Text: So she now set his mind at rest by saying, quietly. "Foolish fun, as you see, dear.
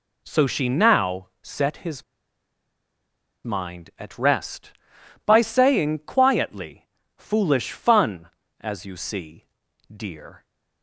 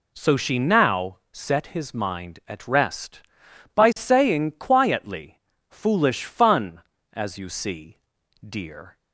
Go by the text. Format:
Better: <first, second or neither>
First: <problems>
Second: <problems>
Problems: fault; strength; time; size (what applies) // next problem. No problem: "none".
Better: second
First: pauses between "his" and "mind"; strong; at 2.0 s; 1.4 s long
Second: none